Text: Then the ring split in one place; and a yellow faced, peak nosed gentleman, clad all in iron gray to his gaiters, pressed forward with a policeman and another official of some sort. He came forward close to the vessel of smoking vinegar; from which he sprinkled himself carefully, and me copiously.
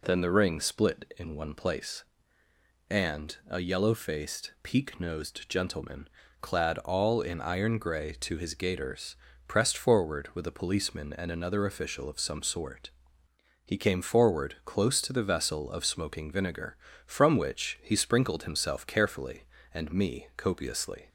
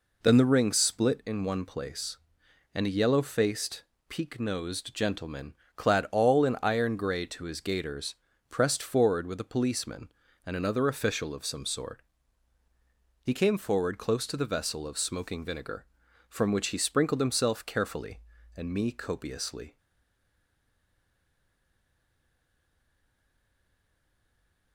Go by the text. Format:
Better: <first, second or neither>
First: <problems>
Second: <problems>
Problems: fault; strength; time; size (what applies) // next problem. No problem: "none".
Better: first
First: none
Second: stays silent after the last word; strong; from 19.7 s on; 5.0 s long